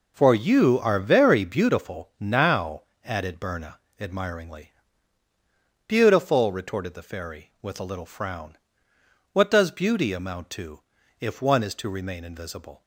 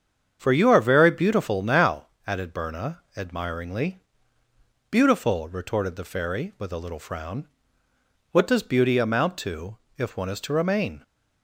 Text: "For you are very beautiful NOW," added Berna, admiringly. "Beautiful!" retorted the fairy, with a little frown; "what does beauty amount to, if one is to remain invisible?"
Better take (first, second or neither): first